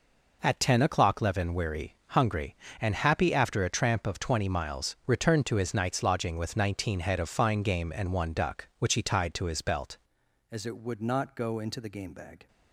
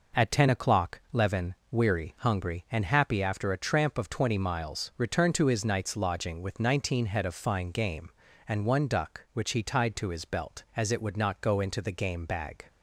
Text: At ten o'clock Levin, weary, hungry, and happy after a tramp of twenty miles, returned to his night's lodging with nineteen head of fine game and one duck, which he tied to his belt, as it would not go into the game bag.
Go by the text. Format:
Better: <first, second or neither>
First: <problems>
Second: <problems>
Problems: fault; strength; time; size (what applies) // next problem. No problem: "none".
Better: second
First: changes voice at "as"; from 10.5 s on; 1.9 s long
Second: none